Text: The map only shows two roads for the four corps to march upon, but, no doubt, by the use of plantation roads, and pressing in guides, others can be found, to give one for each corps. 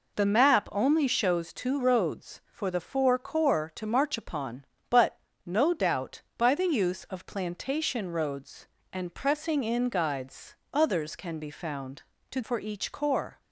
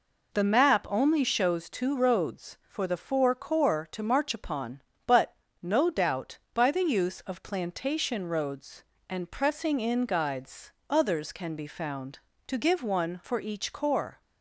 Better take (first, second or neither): second